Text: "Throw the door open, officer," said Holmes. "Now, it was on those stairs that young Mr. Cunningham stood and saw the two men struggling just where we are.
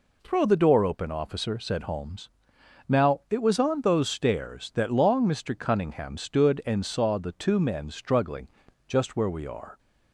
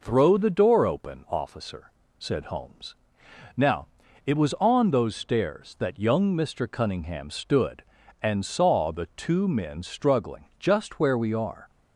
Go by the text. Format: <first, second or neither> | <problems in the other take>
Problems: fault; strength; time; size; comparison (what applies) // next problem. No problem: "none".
second | says "long" for "young"; at 4.9 s // pauses between "struggling" and "just"; at 8.4 s; 0.38 s long